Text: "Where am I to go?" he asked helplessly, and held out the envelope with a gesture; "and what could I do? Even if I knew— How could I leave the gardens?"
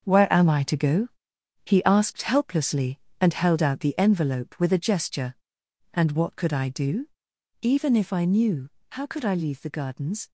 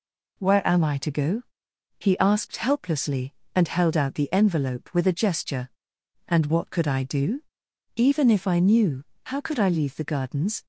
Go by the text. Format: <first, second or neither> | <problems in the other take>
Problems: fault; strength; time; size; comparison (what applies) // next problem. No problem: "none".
second | gets quieter; strong; throughout; 9.5 dB